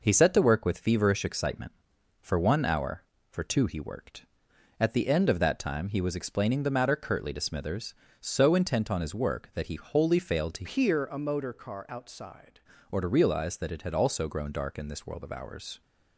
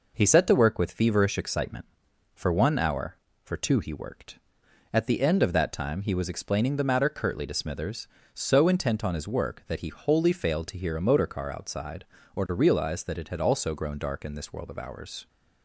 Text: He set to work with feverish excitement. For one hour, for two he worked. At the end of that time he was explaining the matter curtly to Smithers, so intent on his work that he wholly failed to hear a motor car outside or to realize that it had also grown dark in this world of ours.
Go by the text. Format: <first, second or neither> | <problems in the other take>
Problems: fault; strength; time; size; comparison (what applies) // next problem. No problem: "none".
second | changes voice from "hear" to "outside"; from 10.6 to 12.5 s; 1.9 s long